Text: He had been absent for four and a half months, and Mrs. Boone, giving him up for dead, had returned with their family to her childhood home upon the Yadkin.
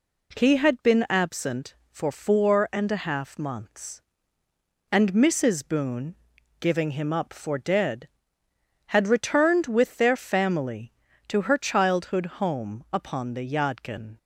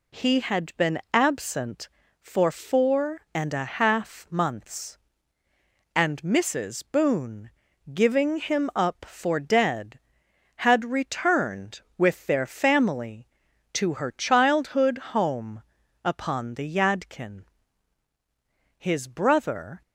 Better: first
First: none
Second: pauses between "childhood" and "home"; slight; at 14.9 s; 0.18 s long // pauses between "home" and "upon"; at 15.6 s; 0.40 s long // goes on to say "His brother"; noticeable; from 18.7 s on; 1.0 s long

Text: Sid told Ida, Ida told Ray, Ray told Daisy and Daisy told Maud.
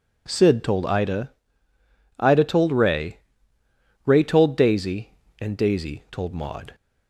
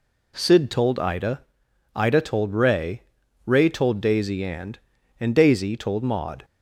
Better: first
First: none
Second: says "and" twice; at 5.2 s

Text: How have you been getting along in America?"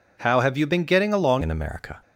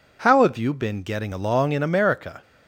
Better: second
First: changes voice at "in"; from 1.4 s on; 0.5 s long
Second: none

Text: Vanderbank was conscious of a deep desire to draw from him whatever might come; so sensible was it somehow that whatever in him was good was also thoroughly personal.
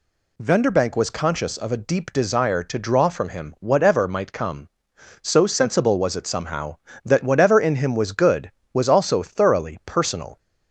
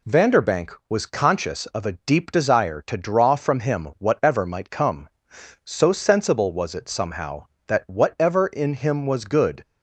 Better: first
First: none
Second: stops before "was also thoroughly personal"; at 9.6 s

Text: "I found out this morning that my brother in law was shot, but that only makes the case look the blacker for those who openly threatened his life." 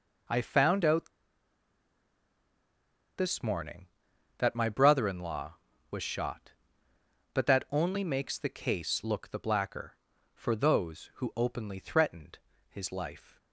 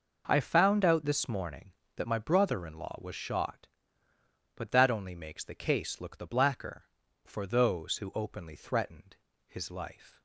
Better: second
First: pauses between "out" and "this"; strong; at 1.0 s; 2.0 s long // pauses between "threatened" and "his"; slight; at 12.3 s; 0.32 s long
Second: pauses between "threatened" and "his"; slight; at 9.1 s; 0.32 s long

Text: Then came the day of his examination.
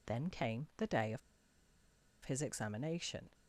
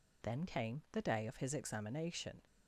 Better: second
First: pauses between "of" and "his"; at 1.2 s; 1.0 s long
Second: none

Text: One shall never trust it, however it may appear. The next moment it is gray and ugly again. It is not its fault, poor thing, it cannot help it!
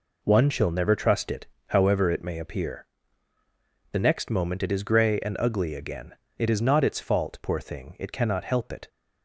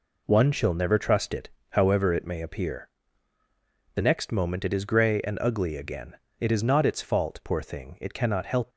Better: first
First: none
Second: stops before "it"; at 8.7 s

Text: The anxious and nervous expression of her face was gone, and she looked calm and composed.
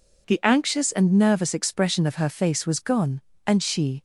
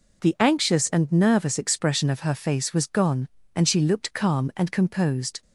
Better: second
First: stops before "looked calm and composed"; at 3.9 s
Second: none

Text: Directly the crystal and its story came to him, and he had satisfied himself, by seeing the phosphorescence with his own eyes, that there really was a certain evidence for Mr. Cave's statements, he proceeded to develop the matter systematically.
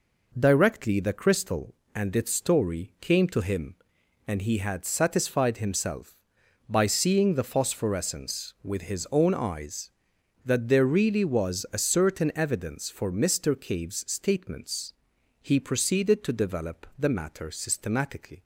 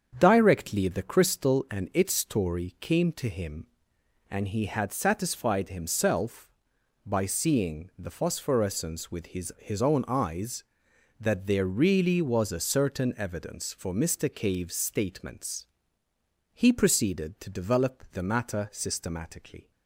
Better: first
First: none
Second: starts louder than the rest; strong; until 1.2 s; 7.5 dB // says "his" twice; at 9.5 s

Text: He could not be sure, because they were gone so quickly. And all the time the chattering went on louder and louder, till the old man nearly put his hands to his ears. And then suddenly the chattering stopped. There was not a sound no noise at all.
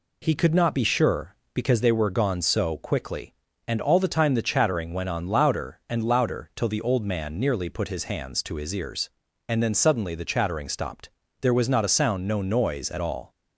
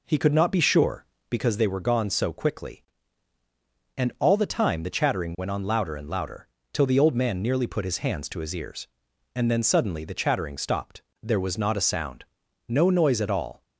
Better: first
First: none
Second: starts louder than the rest; noticeable; until 1.5 s; 4 dB // pauses between "sound" and "no"; noticeable; at 12.2 s; 0.46 s long

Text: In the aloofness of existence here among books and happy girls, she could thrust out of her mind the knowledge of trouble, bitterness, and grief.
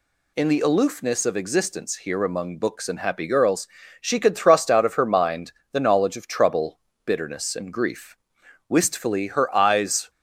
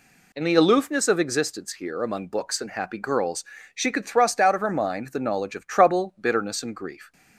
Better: second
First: pauses between "mind" and "the"; slight; at 5.5 s; 0.20 s long // goes on to say "Wistfully her eyes"; from 8.6 s on; 1.4 s long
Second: none

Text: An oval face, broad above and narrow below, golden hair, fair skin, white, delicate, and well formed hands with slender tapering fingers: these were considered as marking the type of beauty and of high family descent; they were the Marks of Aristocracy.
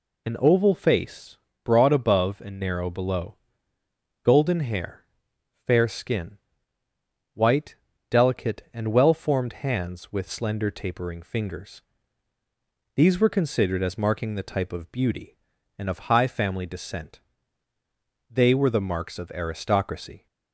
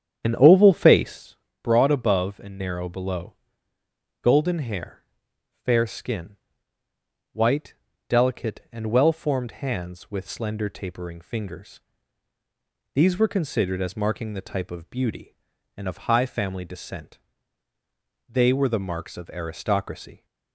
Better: first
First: none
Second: starts louder than the rest; strong; until 1.2 s; 9 dB

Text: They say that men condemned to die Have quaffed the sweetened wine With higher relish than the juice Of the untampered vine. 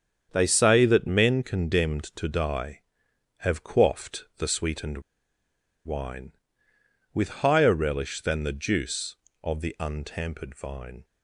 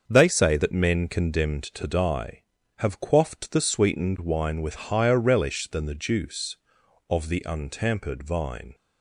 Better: second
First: starts louder than the rest; strong; until 1.3 s; 8 dB // pauses between "sweetened" and "wine"; noticeable; at 4.9 s; 0.85 s long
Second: starts louder than the rest; until 1.1 s; 6.5 dB

